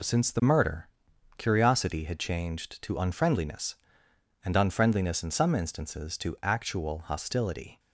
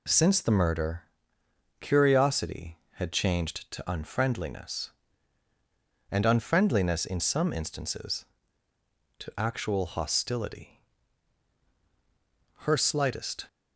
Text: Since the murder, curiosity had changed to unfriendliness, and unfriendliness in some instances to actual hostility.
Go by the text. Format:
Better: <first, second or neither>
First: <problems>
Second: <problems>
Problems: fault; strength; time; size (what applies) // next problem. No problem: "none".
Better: first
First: none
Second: goes on to say "Her slightest"; noticeable; from 12.5 s on; 0.88 s long